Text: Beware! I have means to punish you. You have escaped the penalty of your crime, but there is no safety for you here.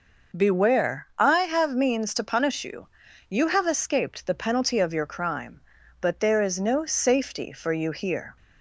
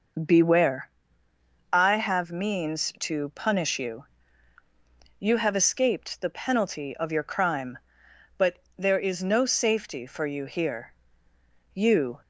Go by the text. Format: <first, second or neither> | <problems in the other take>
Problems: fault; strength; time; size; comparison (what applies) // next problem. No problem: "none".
first | pauses between "but" and "there"; slight; at 8.6 s; 0.18 s long // goes on to say "You"; slight; from 11.7 s on; 0.46 s long